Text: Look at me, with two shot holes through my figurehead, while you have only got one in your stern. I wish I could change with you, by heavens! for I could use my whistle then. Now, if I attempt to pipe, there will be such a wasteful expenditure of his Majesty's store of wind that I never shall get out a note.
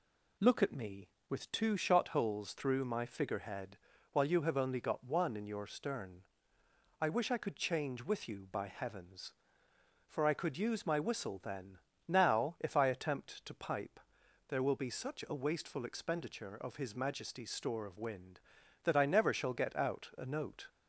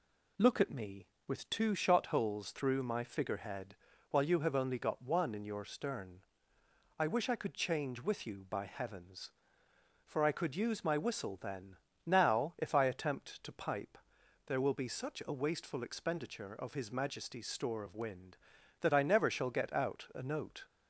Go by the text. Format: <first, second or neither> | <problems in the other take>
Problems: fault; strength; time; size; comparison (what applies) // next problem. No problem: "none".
neither | none